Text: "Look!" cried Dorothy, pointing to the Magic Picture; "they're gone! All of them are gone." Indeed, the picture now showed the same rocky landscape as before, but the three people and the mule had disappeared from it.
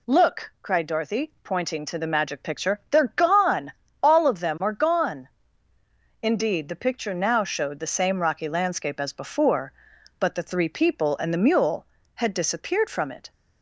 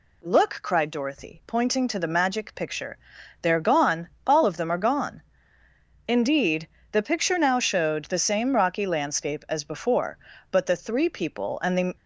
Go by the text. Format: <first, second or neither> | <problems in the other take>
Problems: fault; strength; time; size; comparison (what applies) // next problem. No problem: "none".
first | stops before "mule had disappeared from it"; at 11.9 s